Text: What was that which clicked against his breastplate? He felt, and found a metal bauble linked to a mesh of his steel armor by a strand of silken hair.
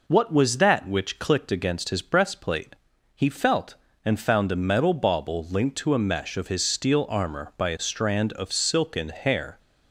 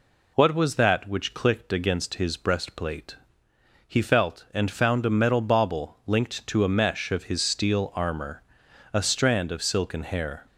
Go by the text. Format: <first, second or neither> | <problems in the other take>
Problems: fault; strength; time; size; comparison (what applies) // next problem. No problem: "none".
first | skips "by"; at 8.6 s